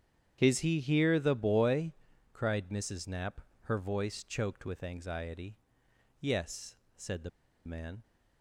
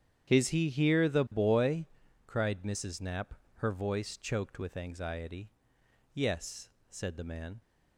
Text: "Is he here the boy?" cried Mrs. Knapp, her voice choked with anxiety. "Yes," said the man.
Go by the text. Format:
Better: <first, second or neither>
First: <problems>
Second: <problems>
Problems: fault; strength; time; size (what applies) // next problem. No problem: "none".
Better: second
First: starts louder than the rest; strong; until 1.4 s; 9 dB // pauses between "the" and "man"; at 7.2 s; 0.36 s long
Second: starts louder than the rest; strong; until 1.3 s; 9 dB